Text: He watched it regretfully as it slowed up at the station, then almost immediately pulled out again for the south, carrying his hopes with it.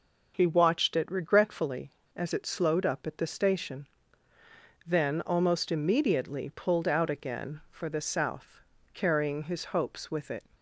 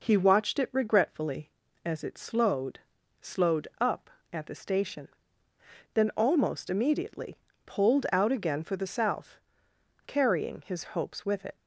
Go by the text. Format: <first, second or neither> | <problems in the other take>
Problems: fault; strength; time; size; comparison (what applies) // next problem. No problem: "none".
first | says "slowed" twice; at 3.2 s // pauses between "immediately" and "pulled"; slight; at 7.3 s; 0.26 s long